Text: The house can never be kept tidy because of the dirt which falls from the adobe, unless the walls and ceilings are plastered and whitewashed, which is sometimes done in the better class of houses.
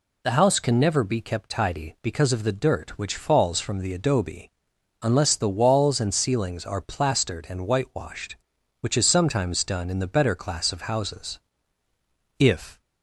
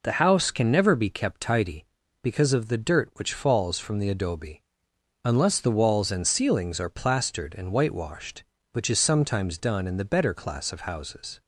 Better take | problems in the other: second | goes on to say "If"; slight; from 12.3 s on; 0.42 s long

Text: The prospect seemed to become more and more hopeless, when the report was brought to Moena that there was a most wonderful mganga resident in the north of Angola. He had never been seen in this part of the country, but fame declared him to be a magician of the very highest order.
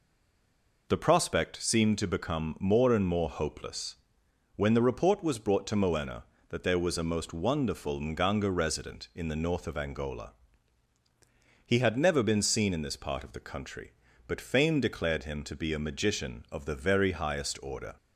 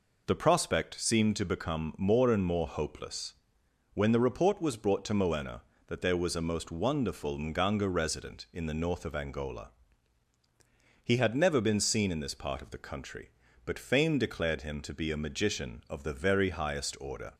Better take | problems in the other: second | stays silent before the first word; slight; until 0.8 s; 0.8 s long

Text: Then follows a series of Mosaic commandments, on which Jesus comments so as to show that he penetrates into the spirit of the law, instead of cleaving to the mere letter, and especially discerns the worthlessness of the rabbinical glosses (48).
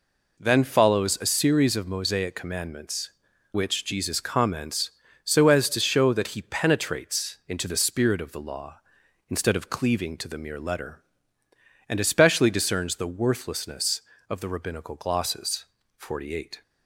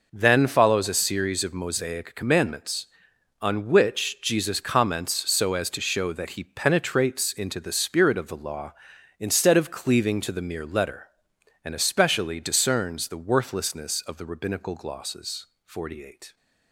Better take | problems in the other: second | skips "on"; at 3.3 s

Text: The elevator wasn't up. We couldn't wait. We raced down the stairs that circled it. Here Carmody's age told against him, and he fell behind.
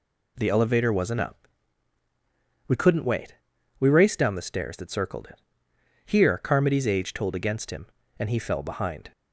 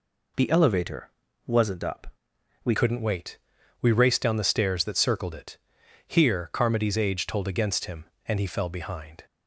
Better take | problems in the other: first | pauses between "elevator" and "wasn't"; slight; at 1.0 s; 0.36 s long // changes voice at "couldn't"; from 2.7 s on; 6.5 s long

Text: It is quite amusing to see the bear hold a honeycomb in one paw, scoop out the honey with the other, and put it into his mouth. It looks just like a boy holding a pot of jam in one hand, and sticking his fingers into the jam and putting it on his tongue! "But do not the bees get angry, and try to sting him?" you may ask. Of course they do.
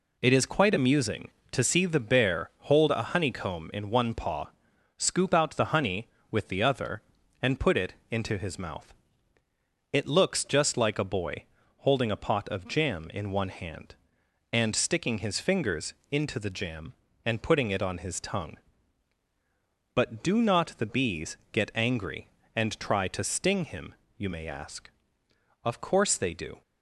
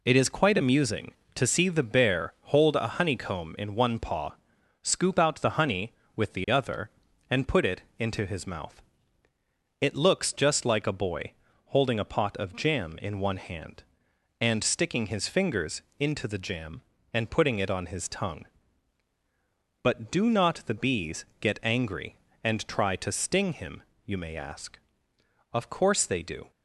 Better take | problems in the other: neither | pauses between "it" and "into"; slight; the same in both // pauses between "boy" and "holding"; slight; the same in both // pauses between "fingers" and "into"; slight; the same in both // pauses between "bees" and "get"; slight; the same in both

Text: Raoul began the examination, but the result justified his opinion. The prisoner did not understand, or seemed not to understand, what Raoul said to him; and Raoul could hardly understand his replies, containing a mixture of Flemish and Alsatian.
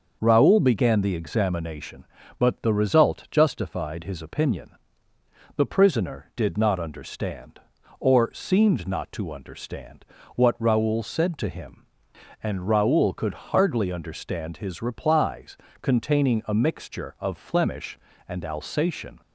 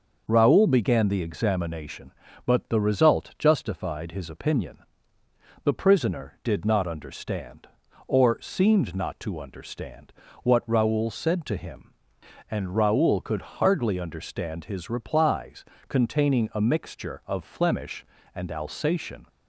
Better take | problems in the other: neither | starts louder than the rest; noticeable; the same in both

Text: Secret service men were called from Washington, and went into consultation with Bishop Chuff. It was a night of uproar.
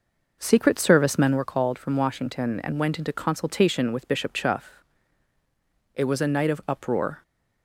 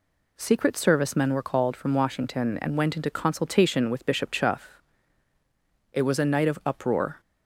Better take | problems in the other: second | starts louder than the rest; noticeable; until 1.5 s; 5.5 dB

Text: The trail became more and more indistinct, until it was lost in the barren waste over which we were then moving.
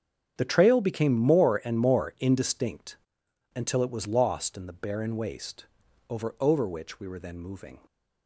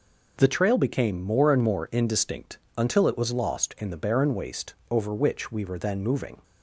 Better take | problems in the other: second | starts louder than the rest; strong; until 1.4 s; 8 dB // pauses between "waste" and "over"; at 5.6 s; 0.42 s long; slight in the second // says "over" twice; at 6.4 s

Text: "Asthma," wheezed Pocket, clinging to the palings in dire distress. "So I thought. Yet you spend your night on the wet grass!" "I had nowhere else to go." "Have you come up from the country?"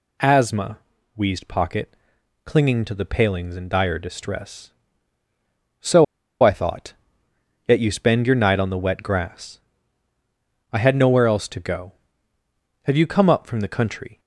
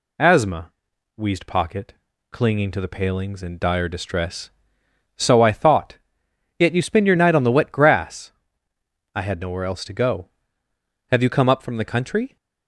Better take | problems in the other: second | pauses between "So" and "I"; at 6.0 s; 0.38 s long

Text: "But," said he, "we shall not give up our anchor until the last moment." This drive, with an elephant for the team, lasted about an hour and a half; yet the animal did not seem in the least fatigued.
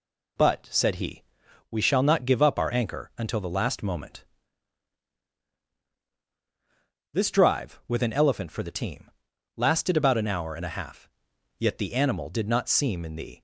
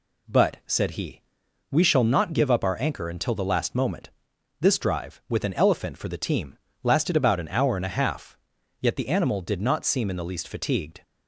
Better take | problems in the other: second | stops before "least fatigued"; at 13.3 s

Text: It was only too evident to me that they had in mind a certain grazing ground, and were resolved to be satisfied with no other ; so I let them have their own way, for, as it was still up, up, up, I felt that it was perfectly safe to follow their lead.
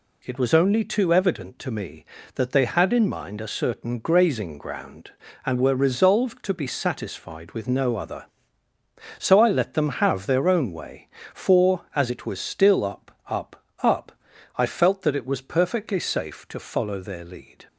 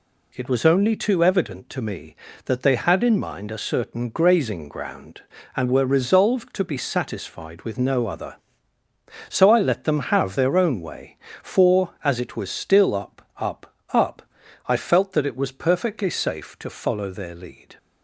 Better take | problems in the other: neither | none

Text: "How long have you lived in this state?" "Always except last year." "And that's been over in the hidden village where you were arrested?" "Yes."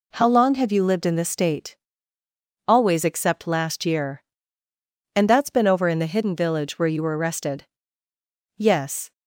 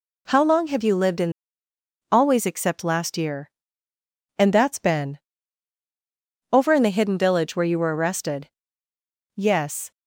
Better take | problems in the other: first | skips "this state"; at 1.6 s // pauses between "been" and "over"; strong; at 5.1 s; 1.3 s long

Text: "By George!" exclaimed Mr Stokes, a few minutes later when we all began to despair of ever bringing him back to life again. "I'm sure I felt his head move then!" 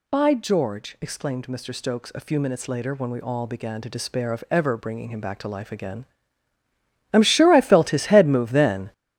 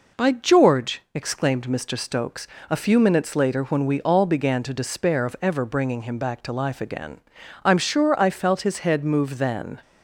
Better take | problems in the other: second | gets louder; strong; throughout; 8.5 dB

